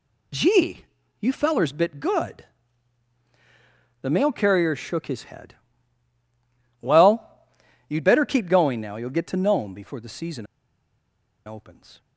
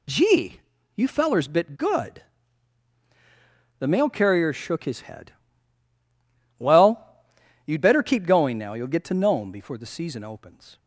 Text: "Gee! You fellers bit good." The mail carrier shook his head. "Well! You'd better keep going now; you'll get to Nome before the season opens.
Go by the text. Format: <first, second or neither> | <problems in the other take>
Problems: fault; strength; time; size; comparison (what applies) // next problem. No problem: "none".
second | pauses between "season" and "opens"; at 10.4 s; 1.0 s long